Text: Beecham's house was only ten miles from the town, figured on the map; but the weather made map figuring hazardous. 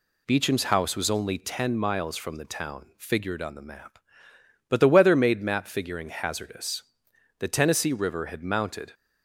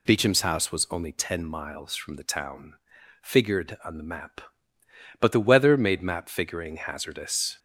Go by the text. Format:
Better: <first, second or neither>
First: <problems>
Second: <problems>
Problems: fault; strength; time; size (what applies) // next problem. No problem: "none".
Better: second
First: goes on to say "The Tennessee River had mounted"; from 7.3 s on; 1.5 s long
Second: none